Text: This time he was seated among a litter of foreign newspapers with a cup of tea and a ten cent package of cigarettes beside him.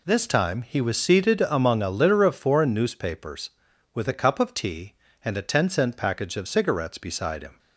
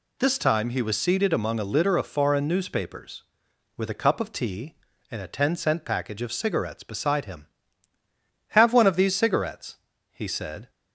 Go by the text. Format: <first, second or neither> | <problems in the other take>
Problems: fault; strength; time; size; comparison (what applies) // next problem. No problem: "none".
first | goes on to say "Have one of these cigarettes he said"; strong; from 8.4 s on; 2.2 s long